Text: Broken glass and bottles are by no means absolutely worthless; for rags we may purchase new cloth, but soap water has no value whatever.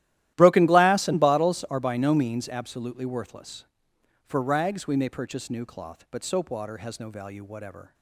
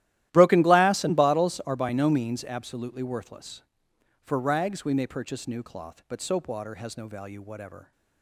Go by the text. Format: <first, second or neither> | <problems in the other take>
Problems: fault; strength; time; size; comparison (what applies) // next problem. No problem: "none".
neither | starts louder than the rest; strong; the same in both